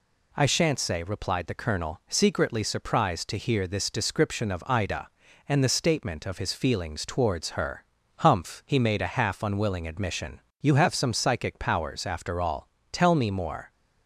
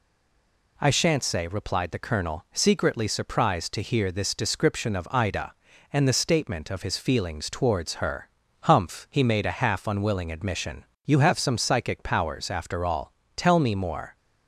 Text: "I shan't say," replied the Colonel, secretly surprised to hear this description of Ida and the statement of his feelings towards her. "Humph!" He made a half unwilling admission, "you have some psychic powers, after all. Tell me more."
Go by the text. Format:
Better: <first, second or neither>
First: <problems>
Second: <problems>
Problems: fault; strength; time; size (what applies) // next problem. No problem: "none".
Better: first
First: none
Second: stays silent before the first word; slight; until 0.7 s; 0.7 s long